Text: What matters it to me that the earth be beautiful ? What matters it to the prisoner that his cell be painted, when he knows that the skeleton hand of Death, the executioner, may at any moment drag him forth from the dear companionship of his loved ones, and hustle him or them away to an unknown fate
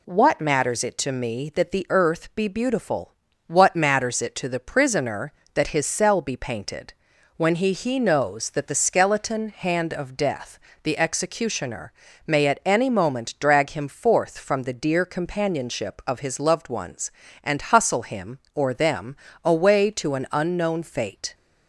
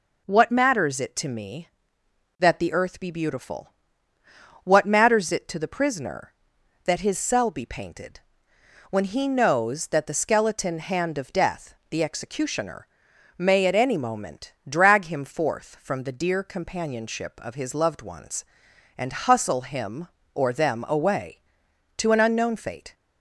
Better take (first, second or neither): second